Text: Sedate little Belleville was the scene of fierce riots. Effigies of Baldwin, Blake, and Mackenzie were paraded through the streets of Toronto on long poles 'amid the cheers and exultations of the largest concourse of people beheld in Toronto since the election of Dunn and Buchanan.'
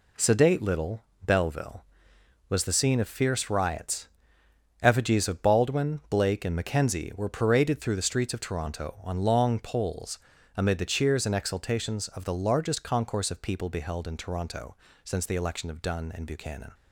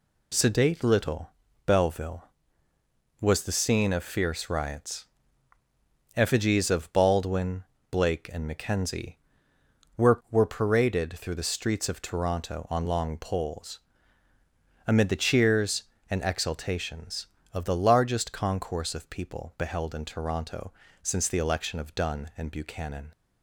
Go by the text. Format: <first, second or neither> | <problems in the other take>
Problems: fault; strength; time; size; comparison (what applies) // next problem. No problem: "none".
first | pauses between "little" and "Belleville"; at 1.2 s; 0.38 s long; slight in the first // says "were" twice; at 10.3 s // pauses between "poles" and "amid"; at 13.7 s; 1.0 s long; slight in the first // pauses between "Toronto" and "since"; slight; at 20.7 s; 0.32 s long; slight in the first